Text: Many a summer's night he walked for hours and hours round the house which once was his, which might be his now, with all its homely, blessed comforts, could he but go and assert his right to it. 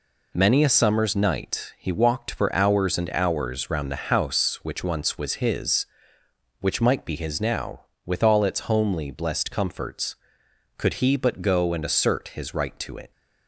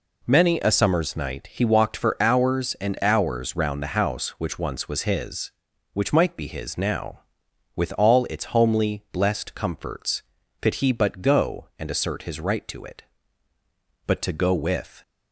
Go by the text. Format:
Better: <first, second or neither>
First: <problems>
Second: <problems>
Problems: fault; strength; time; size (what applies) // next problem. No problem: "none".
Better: first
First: none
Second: goes on to say "But to go with"; noticeable; from 14.0 s on; 0.94 s long